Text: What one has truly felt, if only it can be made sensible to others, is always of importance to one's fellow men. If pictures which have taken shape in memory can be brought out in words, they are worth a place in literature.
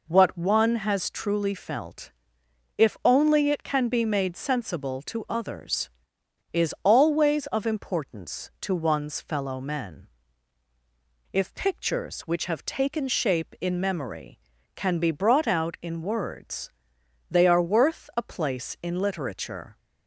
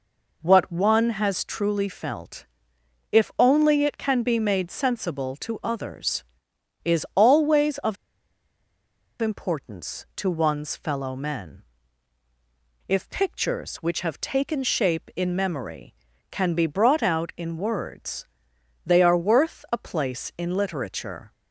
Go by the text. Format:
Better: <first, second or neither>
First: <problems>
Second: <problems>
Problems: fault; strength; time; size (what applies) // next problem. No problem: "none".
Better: first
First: none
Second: pauses between "of" and "importance"; strong; at 7.9 s; 1.2 s long